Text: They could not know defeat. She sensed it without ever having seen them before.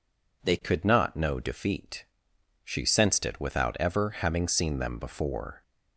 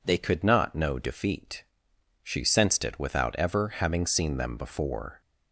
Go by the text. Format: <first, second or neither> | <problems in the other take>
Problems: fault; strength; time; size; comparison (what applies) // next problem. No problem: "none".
neither | none